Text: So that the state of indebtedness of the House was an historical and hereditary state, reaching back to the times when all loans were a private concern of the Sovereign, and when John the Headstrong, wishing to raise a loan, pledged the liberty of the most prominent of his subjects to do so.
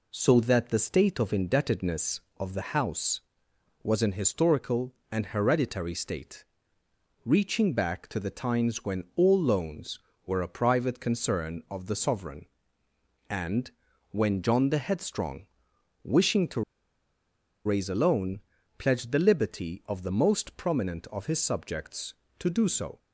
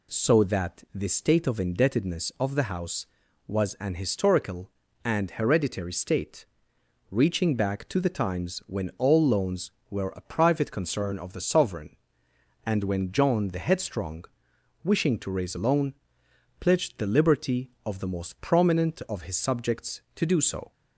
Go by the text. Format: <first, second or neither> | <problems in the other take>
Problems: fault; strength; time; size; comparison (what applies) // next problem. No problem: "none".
second | pauses between "and" and "when"; at 13.7 s; 0.40 s long // pauses between "to" and "raise"; at 16.6 s; 1.0 s long